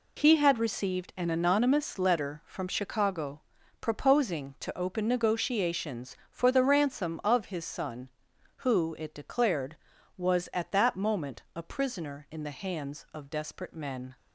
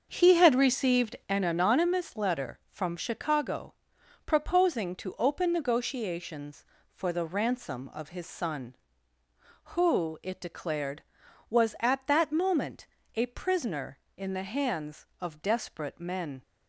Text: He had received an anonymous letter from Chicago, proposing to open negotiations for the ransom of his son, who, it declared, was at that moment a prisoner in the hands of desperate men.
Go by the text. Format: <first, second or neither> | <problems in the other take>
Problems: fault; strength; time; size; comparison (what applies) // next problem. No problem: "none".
first | starts louder than the rest; until 1.3 s; 6.5 dB // pauses between "moment" and "a"; slight; at 12.8 s; 0.26 s long